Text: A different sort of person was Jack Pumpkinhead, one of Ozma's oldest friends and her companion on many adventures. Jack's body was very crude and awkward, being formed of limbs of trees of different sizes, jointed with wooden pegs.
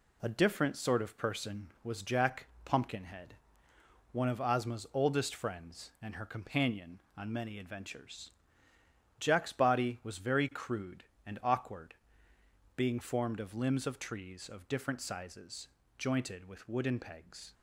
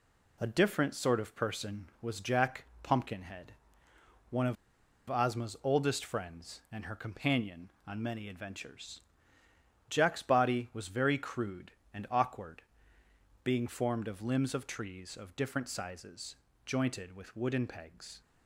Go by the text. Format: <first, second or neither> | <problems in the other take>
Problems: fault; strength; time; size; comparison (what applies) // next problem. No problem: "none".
first | pauses between "Jack" and "Pumpkinhead"; slight; at 2.6 s; 0.18 s long; slight in the first // pauses between "of" and "Ozma's"; noticeable; at 4.5 s; 0.53 s long